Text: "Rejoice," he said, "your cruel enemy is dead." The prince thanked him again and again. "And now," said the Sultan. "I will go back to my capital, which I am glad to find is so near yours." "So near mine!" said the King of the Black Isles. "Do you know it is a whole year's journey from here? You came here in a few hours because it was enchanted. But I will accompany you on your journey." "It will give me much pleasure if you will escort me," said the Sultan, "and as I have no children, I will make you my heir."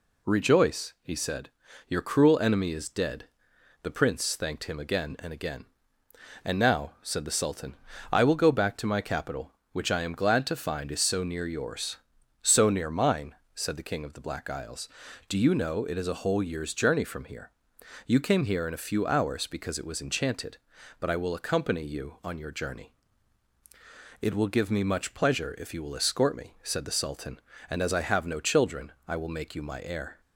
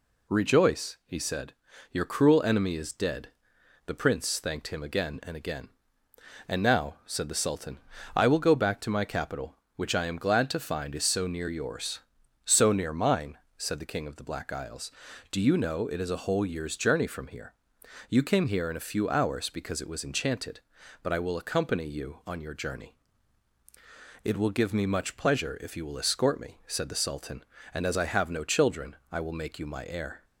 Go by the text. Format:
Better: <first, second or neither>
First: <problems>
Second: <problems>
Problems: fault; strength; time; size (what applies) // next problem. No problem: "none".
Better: neither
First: none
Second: none